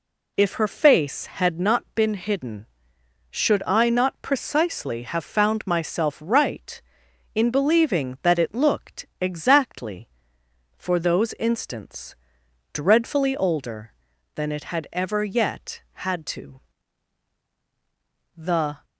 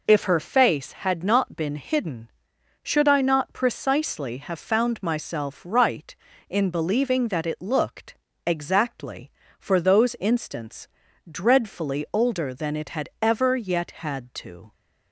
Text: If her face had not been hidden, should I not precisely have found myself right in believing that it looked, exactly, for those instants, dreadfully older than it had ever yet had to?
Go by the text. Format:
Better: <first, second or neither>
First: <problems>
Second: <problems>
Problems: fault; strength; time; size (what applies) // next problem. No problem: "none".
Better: second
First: goes on to say "The"; slight; from 18.3 s on; 0.48 s long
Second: none